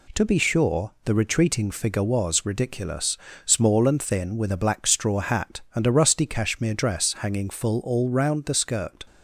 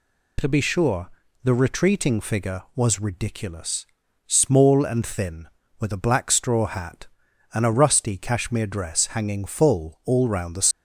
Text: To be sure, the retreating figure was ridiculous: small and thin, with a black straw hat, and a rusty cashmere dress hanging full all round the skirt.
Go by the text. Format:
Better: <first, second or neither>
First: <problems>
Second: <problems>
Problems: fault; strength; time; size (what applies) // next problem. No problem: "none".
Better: first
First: none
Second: stops before "skirt"; at 10.7 s